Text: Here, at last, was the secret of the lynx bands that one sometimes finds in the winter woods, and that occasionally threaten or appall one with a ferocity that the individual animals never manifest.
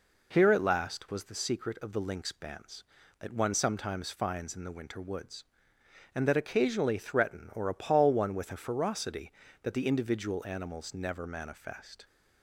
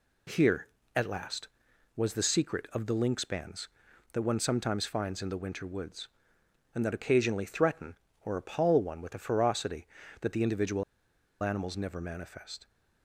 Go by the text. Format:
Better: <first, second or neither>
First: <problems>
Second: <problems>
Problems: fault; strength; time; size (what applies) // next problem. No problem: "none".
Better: first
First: none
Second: pauses between "individual" and "animals"; noticeable; at 10.8 s; 0.57 s long